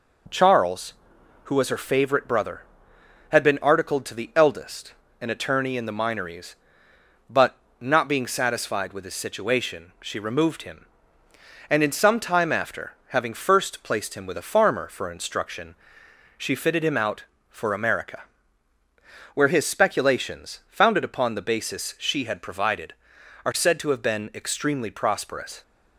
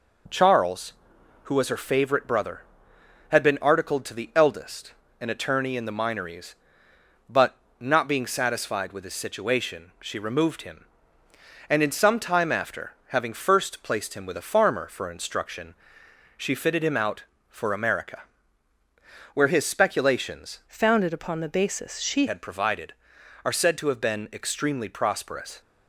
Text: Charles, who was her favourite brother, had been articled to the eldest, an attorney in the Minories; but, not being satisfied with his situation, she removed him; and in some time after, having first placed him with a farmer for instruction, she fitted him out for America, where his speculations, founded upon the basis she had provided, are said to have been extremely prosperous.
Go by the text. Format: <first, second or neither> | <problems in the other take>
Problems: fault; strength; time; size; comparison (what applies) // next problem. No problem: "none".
first | changes voice from "founded" to "she"; from 20.6 to 22.2 s; 1.6 s long